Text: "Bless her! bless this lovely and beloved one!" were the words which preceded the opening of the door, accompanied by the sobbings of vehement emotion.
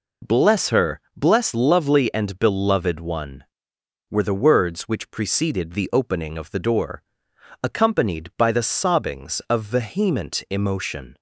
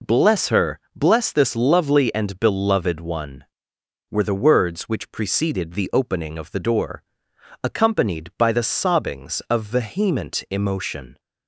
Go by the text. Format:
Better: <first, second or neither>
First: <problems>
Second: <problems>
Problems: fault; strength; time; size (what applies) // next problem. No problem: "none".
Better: second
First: skips "this"; at 1.5 s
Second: none